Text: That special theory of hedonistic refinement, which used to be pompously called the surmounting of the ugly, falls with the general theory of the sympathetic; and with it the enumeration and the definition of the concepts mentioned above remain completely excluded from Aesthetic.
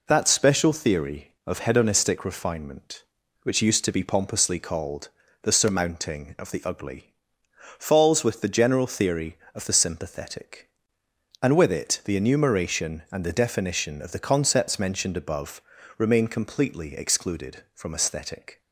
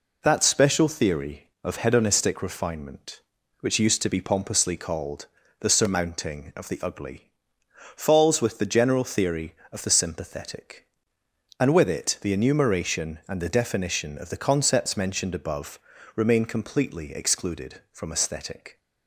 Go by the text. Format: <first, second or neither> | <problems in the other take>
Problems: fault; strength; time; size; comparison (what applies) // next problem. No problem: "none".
neither | pauses between "called" and "the"; slight; the same in both // pauses between "above" and "remain"; slight; the same in both